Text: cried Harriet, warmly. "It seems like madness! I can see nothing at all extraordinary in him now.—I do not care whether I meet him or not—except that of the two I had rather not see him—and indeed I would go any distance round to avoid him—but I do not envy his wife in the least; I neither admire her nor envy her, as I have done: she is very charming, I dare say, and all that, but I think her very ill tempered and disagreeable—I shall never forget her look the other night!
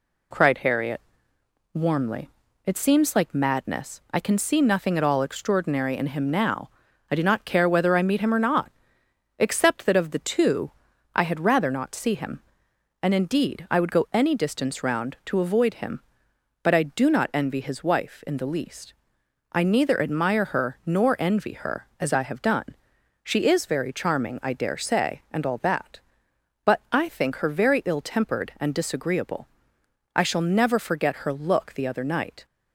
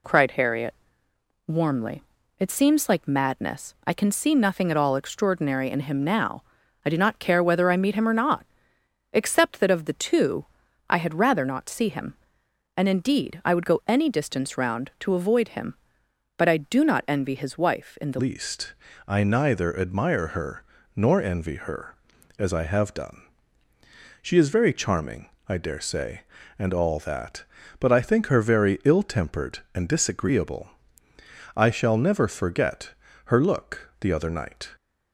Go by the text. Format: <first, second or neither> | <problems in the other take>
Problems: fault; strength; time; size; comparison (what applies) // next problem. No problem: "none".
first | pauses between "two" and "I"; at 10.4 s; 0.42 s long; also in the first // changes voice at "least"; from 18.1 s on; 16.6 s long // pauses between "her" and "nor"; slight; at 20.6 s; 0.32 s long // pauses between "forget" and "her"; slight; at 32.9 s; 0.32 s long